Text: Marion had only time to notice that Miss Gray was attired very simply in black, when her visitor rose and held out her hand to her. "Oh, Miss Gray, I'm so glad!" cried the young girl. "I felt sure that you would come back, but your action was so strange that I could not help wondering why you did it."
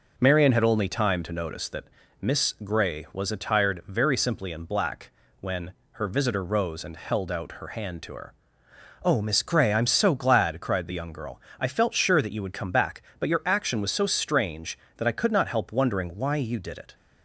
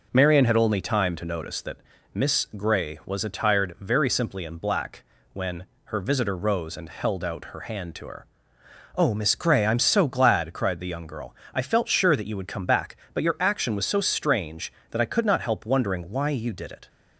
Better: neither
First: pauses between "that" and "Miss"; at 1.8 s; 0.38 s long // pauses between "when" and "her"; slight; at 5.7 s; 0.20 s long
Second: pauses between "that" and "Miss"; at 1.7 s; 0.38 s long // pauses between "when" and "her"; slight; at 5.6 s; 0.20 s long

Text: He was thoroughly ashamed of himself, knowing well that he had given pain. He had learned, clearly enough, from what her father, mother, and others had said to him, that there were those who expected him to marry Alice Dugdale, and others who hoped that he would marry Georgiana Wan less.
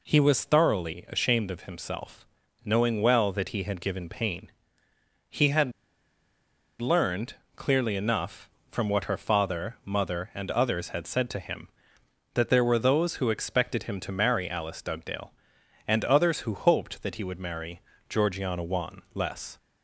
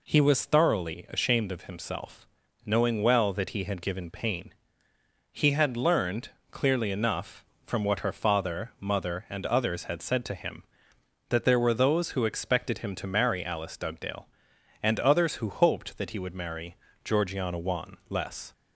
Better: second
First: pauses between "had" and "learned"; at 5.7 s; 1.0 s long // pauses between "marry" and "Georgiana"; slight; at 17.8 s; 0.28 s long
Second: pauses between "marry" and "Georgiana"; slight; at 16.7 s; 0.28 s long

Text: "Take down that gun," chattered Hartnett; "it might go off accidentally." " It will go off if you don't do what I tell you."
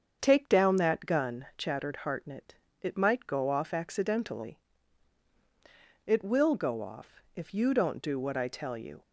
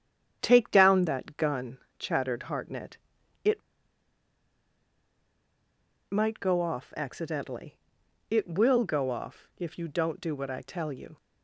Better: first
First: starts louder than the rest; strong; until 1.2 s; 8 dB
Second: starts louder than the rest; strong; until 1.4 s; 9 dB // pauses between "it" and "might"; strong; at 3.6 s; 2.4 s long

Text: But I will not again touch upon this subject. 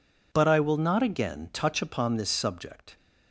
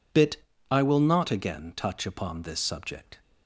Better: first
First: none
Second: says "Bit" for "But"; at 0.1 s

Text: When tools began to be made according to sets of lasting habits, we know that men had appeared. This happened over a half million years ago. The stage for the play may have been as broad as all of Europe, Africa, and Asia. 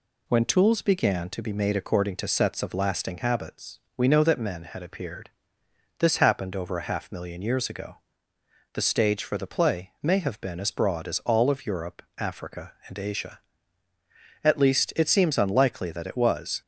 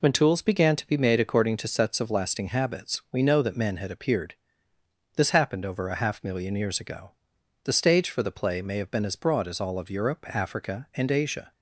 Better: second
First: goes on to say "At least it seems unlikely that it was"; strong; from 14.4 s on; 2.1 s long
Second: none

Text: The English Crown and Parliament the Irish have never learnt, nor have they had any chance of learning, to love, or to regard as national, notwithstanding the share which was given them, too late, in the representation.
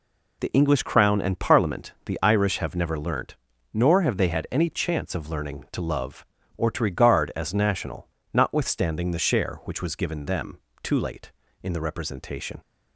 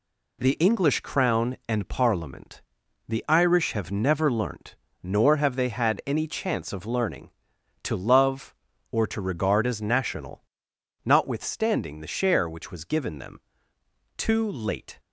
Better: first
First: none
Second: pauses between "Parliament" and "the"; at 2.6 s; 0.44 s long // stops before "in the representation"; at 14.9 s

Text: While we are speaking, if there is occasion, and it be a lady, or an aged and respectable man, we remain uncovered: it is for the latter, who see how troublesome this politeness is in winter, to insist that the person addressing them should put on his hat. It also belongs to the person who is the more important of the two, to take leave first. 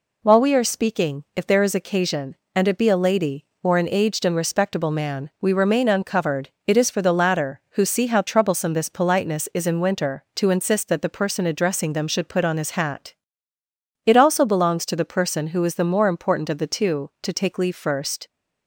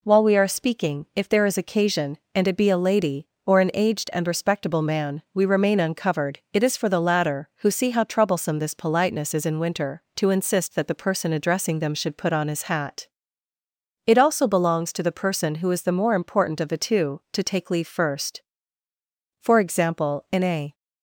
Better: first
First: none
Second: goes on to say "For example in a"; from 19.4 s on; 1.3 s long

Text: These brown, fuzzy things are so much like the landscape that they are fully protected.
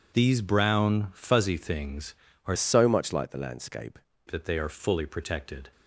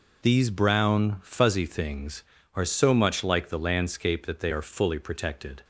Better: second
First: changes voice from "so" to "landscape"; from 2.5 to 3.9 s; 1.4 s long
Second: none

